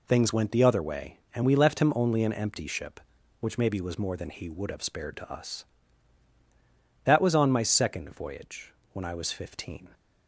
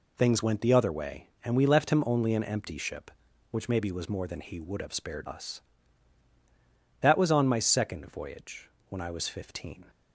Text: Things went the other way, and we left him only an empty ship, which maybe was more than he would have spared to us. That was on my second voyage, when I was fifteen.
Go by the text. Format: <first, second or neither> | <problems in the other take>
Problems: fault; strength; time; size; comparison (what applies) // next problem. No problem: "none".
first | skips "to"; at 5.2 s